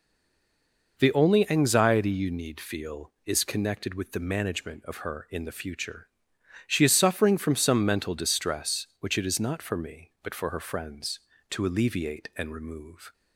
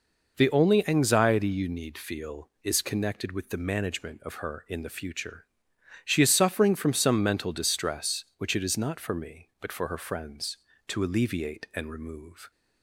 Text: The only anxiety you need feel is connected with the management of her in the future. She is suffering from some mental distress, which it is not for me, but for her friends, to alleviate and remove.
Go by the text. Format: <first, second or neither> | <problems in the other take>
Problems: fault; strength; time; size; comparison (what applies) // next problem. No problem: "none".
second | stays silent before the first word; until 0.9 s; 0.9 s long